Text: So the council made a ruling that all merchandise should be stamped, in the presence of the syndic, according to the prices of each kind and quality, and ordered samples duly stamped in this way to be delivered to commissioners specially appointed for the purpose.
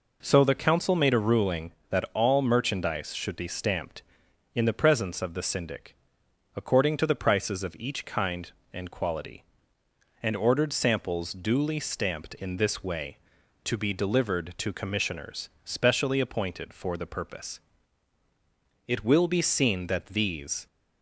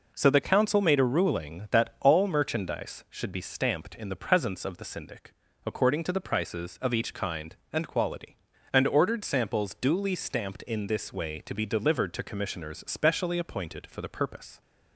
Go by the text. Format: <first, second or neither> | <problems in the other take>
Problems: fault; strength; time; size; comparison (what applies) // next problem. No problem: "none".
second | goes on to say "It will be seen that these"; strong; from 18.8 s on; 1.7 s long